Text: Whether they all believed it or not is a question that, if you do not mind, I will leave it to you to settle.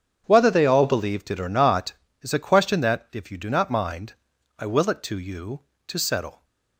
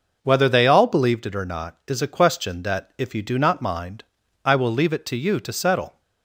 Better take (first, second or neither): second